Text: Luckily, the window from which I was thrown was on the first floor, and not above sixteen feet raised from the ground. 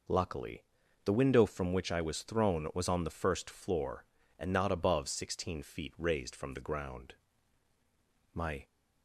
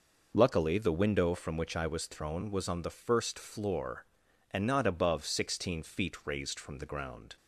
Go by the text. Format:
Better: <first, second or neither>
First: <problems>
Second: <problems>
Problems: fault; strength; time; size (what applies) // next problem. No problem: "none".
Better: second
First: goes on to say "My"; slight; from 8.3 s on; 0.34 s long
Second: none